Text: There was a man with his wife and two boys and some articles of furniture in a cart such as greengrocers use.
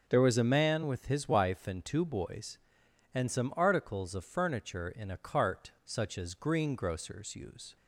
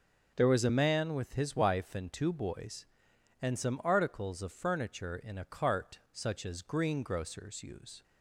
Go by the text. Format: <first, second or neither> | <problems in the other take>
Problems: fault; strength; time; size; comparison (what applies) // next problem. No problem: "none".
neither | none